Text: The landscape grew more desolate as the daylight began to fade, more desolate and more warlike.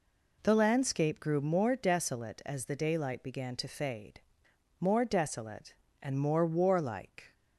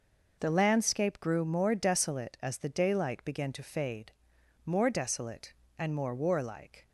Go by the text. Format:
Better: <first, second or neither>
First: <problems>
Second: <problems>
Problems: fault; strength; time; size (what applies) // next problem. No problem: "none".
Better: neither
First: none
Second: none